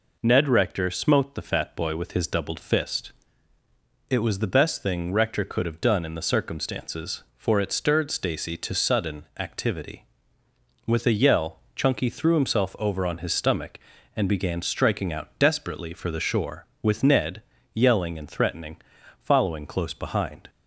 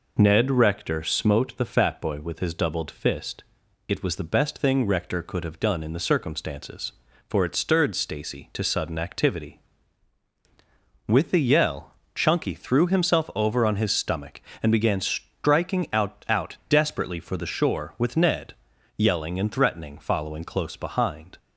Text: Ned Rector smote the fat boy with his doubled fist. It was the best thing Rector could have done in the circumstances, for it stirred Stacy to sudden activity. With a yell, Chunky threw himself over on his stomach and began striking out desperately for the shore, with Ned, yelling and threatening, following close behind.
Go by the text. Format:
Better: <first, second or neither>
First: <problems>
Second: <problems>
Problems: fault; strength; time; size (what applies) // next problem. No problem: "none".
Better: first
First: none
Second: says "out" twice; at 16.2 s